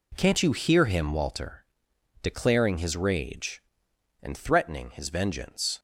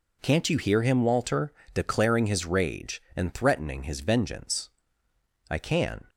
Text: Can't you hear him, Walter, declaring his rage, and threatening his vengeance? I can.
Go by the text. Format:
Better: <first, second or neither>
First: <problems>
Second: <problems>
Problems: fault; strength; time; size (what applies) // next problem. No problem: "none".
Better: second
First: stops before "I can"; at 5.7 s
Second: none